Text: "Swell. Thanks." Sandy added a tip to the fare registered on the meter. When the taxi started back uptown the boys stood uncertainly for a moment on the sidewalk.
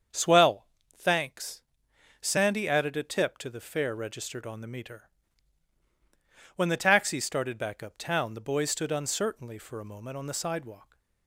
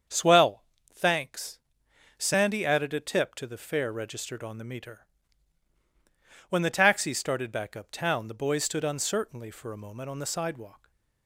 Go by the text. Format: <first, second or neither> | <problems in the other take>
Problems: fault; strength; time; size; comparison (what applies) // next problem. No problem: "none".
neither | starts louder than the rest; strong; the same in both